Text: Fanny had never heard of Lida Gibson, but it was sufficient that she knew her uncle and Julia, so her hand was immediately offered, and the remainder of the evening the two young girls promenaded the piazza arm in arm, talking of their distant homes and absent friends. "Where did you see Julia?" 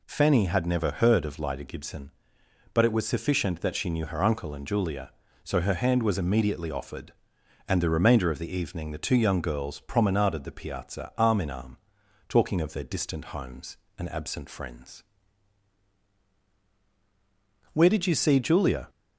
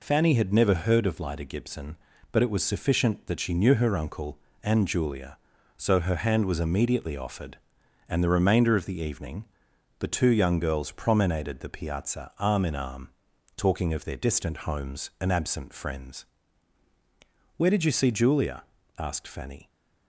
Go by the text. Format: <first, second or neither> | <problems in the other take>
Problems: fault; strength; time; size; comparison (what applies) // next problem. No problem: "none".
first | pauses between "evening" and "the"; noticeable; at 9.4 s; 0.56 s long // goes on to say "asked Fanny"; noticeable; from 18.9 s on; 0.70 s long